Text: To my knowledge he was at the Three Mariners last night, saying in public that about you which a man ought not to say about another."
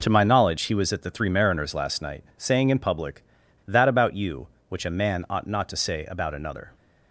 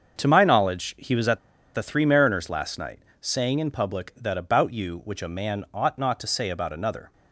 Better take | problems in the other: first | starts louder than the rest; until 1.2 s; 6.5 dB // pauses between "at" and "the"; slight; at 1.3 s; 0.35 s long

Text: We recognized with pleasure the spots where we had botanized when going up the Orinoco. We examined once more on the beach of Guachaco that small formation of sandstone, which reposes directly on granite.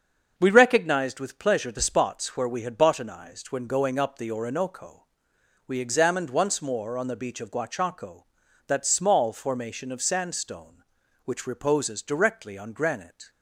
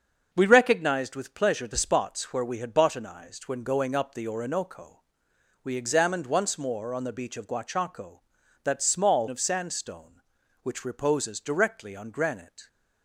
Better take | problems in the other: first | starts louder than the rest; until 1.3 s; 7 dB; also in the first // skips "formation"; at 9.2 s

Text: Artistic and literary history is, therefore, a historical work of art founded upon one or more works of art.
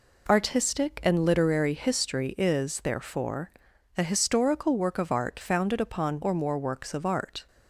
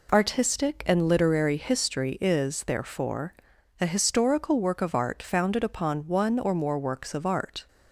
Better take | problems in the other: second | skips "one"; at 6.2 s

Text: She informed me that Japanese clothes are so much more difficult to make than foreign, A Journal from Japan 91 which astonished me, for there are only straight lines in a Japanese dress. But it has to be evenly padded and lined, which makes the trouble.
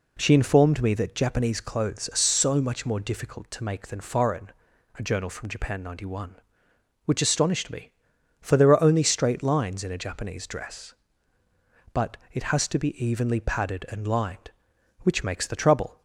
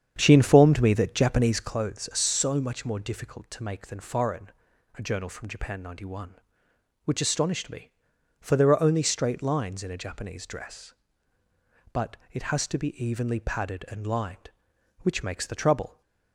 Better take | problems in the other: first | starts louder than the rest; strong; until 1.9 s; 8 dB // pauses between "But" and "it"; slight; at 12.1 s; 0.16 s long; slight in the first

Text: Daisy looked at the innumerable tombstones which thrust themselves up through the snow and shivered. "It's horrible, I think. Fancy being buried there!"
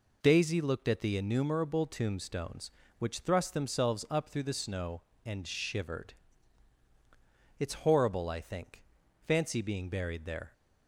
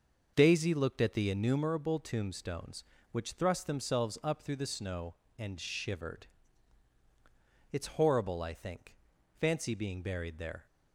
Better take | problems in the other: first | starts louder than the rest; until 1.7 s; 6 dB

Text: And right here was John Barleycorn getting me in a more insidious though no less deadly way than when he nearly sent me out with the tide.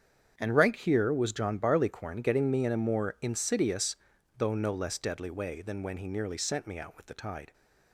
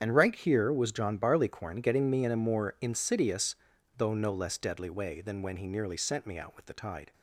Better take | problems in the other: first | loses the start of "And"; at 0.0 s; 40 ms // starts louder than the rest; strong; until 1.0 s; 8 dB; strong in the first // pauses between "insidious" and "though"; at 3.5 s; 0.42 s long; also in the first

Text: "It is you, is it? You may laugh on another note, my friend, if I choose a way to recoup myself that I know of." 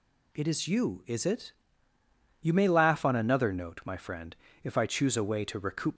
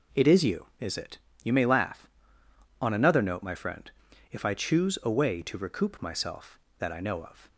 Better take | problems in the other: second | stops before "myself that I know of"; at 5.9 s

